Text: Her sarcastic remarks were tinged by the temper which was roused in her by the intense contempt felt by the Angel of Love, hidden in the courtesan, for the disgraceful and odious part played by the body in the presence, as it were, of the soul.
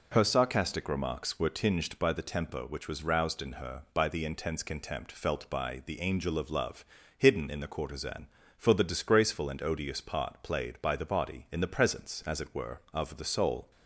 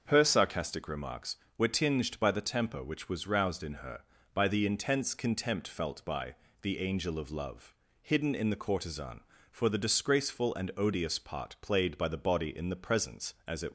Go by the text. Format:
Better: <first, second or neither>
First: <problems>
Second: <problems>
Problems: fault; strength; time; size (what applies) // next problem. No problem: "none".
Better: first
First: none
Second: starts louder than the rest; until 1.0 s; 6.5 dB // pauses between "by" and "the"; slight; at 6.3 s; 0.24 s long // stops before "were of the soul"; at 13.6 s